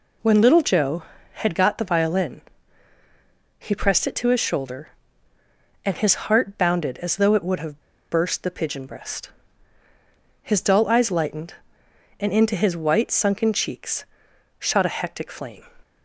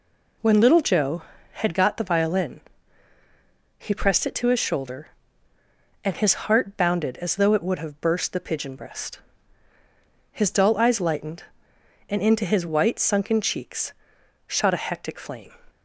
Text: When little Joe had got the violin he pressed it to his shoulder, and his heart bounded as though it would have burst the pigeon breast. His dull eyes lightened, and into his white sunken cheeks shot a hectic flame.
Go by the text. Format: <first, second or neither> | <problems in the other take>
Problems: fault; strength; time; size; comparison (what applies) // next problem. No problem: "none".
second | pauses between "violin" and "he"; at 2.4 s; 1.1 s long; also in the second // pauses between "have" and "burst"; slight; at 7.8 s; 0.29 s long // pauses between "cheeks" and "shot"; noticeable; at 14.0 s; 0.52 s long; noticeable in the second